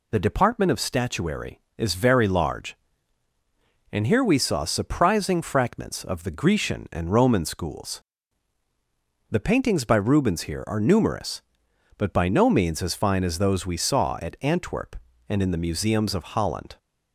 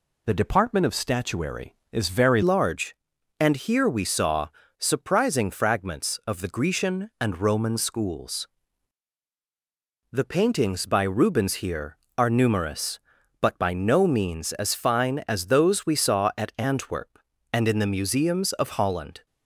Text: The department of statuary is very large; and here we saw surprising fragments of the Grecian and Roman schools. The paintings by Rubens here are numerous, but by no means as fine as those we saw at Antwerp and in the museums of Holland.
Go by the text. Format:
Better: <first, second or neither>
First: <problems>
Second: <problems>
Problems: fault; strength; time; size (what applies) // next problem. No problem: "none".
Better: first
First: none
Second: changes voice at "large"; from 2.4 s on; 16.8 s long // pauses between "saw" and "surprising"; slight; at 4.4 s; 0.32 s long